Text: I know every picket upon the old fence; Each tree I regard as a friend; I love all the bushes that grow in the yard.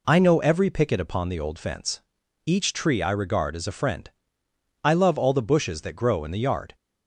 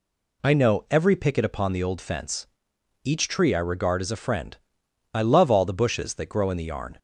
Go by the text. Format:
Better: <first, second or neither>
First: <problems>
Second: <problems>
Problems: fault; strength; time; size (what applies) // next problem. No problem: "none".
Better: first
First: none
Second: says "yarn" for "yard"; at 6.6 s